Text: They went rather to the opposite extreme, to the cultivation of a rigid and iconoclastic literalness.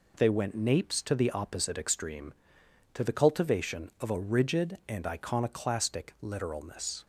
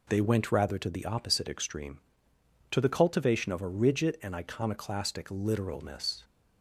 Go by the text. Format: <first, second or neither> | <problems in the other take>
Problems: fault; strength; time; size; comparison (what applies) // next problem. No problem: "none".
second | says "napes" for "rather"; at 0.5 s